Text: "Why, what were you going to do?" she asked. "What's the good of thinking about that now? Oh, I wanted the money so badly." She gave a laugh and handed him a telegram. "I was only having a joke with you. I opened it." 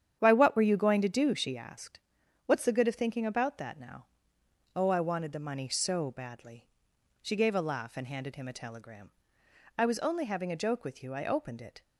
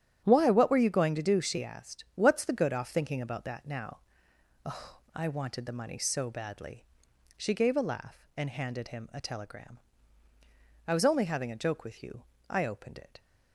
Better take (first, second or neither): first